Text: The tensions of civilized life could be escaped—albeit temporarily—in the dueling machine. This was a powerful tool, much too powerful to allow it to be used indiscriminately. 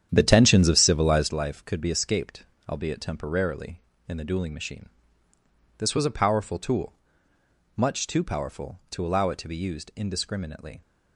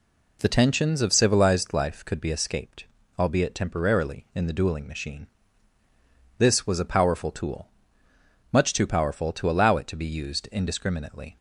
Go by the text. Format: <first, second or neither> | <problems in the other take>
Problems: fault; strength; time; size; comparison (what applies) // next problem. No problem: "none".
second | starts louder than the rest; strong; until 1.4 s; 9.5 dB